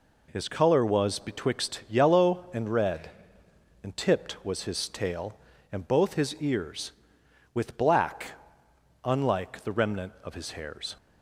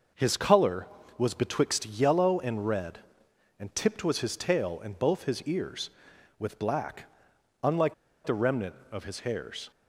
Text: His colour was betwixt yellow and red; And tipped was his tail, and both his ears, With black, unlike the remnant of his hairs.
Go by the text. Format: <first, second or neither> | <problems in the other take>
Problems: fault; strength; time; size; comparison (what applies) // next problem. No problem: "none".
first | pauses between "unlike" and "the"; slight; at 7.9 s; 0.32 s long